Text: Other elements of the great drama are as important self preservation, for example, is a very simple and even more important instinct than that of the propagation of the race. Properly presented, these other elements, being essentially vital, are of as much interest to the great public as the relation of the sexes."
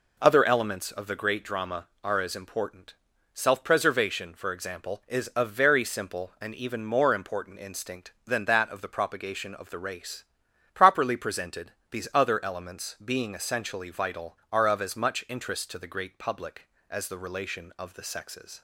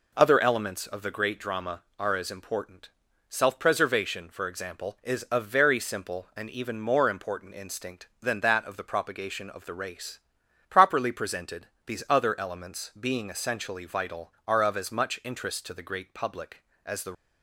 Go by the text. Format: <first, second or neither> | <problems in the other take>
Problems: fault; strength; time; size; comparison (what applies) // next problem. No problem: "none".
first | pauses between "important" and "self"; at 2.9 s; 0.38 s long; also in the first // stops before "relation of the sexes"; at 17.1 s